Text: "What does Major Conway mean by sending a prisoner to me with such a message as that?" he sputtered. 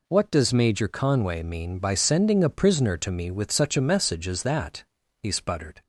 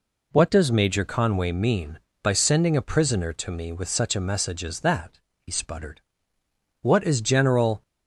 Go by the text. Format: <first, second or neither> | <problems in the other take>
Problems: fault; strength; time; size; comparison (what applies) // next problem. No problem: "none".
first | goes on to say "What is General"; noticeable; from 6.8 s on; 1.0 s long